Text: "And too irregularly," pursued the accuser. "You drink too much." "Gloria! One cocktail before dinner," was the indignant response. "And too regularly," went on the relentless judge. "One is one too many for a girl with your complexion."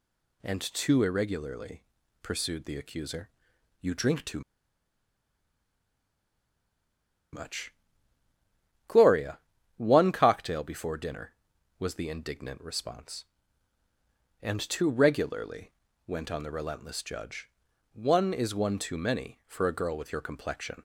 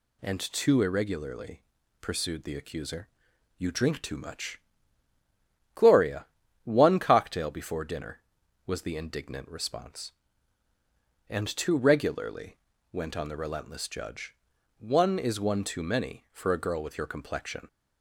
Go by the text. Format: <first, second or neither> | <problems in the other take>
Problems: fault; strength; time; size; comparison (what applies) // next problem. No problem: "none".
second | pauses between "too" and "much"; strong; at 4.3 s; 2.9 s long